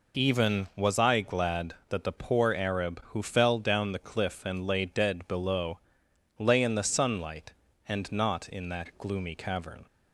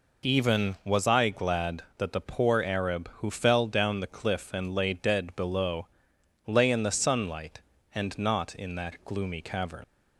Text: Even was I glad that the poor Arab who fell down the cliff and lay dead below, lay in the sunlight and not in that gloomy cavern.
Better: first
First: none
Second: leaves "cavern" unfinished; at 9.8 s; 85 ms

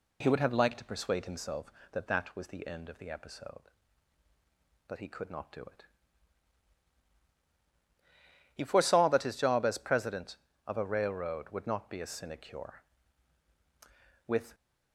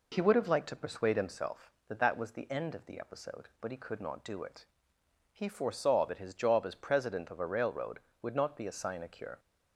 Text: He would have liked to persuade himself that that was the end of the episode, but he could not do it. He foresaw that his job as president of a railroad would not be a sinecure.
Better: second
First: goes on to say "With"; slight; from 14.2 s on; 0.26 s long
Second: none

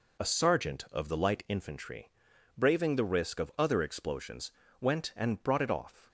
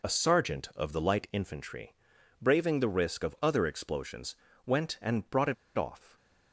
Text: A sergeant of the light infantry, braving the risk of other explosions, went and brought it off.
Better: first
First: none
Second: pauses between "it" and "off"; slight; at 5.5 s; 0.23 s long

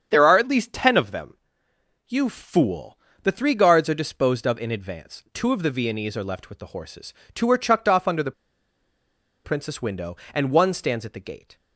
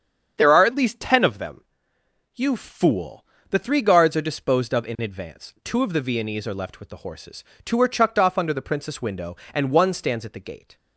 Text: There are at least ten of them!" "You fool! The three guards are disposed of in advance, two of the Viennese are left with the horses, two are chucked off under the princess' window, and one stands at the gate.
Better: second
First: starts louder than the rest; strong; until 1.1 s; 7.5 dB // pauses between "the" and "princess"; at 8.3 s; 1.1 s long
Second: starts louder than the rest; strong; until 1.3 s; 7.5 dB

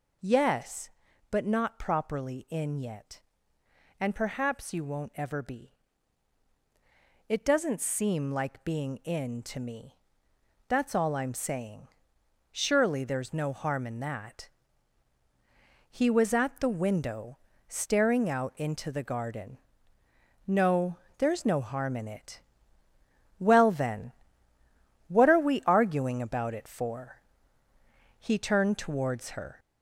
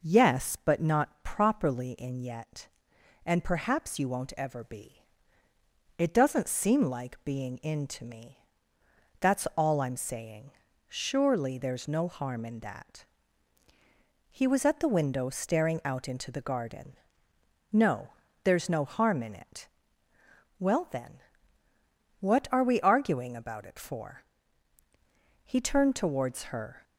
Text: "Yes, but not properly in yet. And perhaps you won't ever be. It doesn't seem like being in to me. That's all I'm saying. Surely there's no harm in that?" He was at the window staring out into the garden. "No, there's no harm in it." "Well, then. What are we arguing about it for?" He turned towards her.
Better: second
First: gets louder; noticeable; throughout; 4 dB // pauses between "window" and "staring"; slight; at 17.3 s; 0.30 s long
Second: none

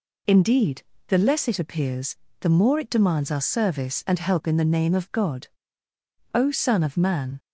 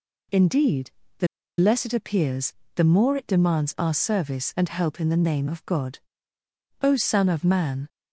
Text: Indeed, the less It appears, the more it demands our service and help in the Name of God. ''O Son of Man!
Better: first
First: none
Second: pauses between "the" and "less"; slight; at 1.2 s; 0.31 s long

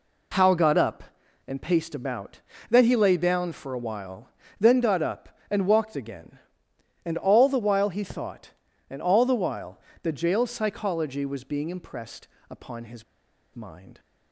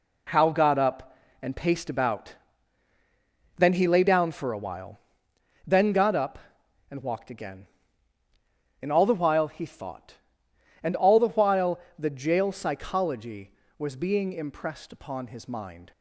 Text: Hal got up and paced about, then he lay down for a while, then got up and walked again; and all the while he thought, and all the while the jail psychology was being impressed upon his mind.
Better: second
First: pauses between "while" and "the"; slight; at 9.7 s; 0.22 s long // pauses between "impressed" and "upon"; slight; at 12.2 s; 0.20 s long // pauses between "his" and "mind"; noticeable; at 13.0 s; 0.51 s long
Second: pauses between "while" and "the"; slight; at 11.7 s; 0.20 s long

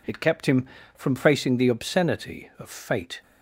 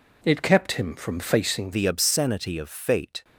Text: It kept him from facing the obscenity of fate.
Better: first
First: none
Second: changes voice at "the"; from 1.7 s on; 1.5 s long

